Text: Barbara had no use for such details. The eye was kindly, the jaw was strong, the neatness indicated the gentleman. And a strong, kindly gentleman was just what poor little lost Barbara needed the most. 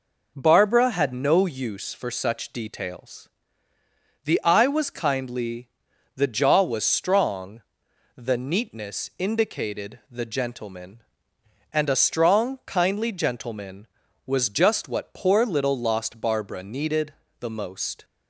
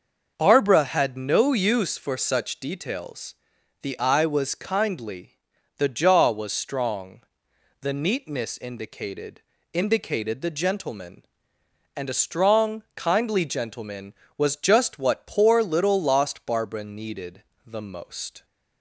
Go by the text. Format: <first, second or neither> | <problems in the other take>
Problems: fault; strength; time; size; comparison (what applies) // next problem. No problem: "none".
first | says "indicated" twice; at 9.7 s // pauses between "needed" and "the"; slight; at 17.4 s; 0.22 s long; slight in the first